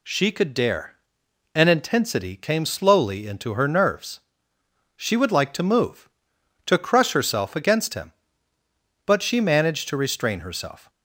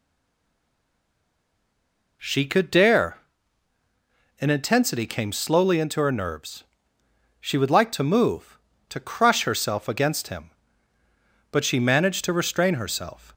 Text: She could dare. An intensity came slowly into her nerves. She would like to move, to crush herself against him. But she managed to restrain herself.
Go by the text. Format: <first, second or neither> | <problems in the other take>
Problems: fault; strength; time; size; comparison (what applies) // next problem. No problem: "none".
first | stays silent before the first word; until 2.2 s; 2.2 s long